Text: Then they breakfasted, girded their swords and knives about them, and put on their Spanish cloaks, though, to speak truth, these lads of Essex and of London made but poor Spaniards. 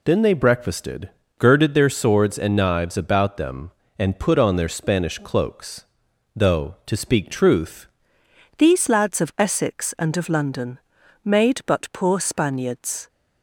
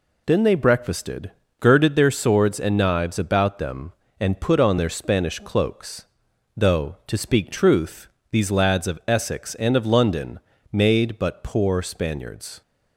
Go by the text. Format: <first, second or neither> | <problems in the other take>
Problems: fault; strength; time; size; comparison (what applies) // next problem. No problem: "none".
second | changes voice at "these"; from 8.5 s on; 4.5 s long // pauses between "London" and "made"; noticeable; at 10.7 s; 0.46 s long; slight in the second